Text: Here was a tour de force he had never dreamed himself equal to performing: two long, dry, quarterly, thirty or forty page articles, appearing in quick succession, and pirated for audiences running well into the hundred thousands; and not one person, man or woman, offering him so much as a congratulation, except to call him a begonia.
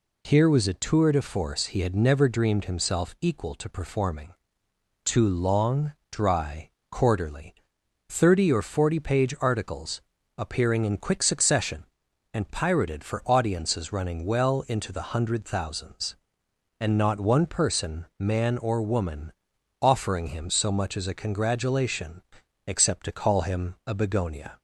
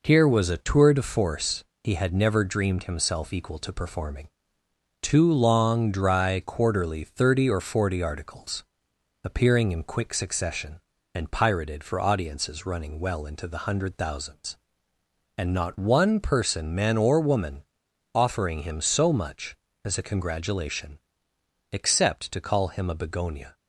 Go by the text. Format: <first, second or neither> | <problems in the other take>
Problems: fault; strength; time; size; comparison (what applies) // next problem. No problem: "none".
first | pauses between "force" and "he"; slight; at 1.6 s; 0.22 s long // skips "page"; at 8.0 s